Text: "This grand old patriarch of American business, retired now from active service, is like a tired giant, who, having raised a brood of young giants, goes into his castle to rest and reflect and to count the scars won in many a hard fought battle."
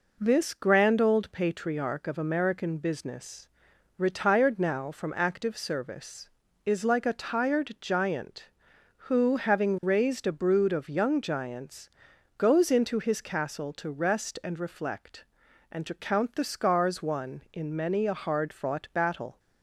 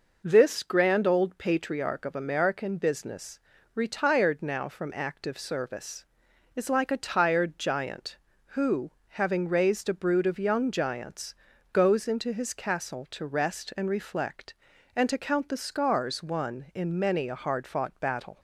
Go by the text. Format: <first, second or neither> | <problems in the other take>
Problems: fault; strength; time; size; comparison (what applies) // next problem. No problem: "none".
neither | none